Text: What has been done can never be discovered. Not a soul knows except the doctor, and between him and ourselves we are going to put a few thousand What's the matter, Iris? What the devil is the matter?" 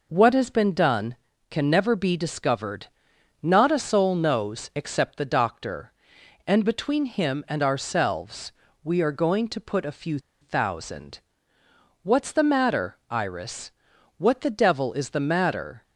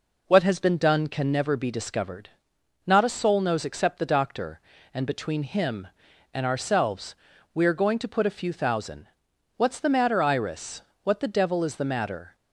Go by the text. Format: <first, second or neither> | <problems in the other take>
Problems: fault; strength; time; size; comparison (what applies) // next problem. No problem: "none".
second | pauses between "ourselves" and "we"; slight; at 8.5 s; 0.32 s long; also in the second // pauses between "few" and "thousand"; slight; at 10.1 s; 0.22 s long // pauses between "thousand" and "What's"; noticeable; at 11.1 s; 0.86 s long; noticeable in the second